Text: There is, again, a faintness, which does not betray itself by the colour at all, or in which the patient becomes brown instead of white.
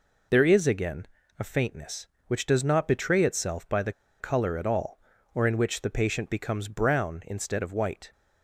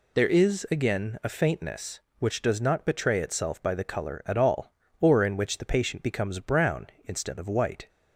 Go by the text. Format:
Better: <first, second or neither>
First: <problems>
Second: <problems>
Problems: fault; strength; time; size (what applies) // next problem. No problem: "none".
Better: second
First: pauses between "the" and "colour"; slight; at 3.9 s; 0.28 s long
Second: none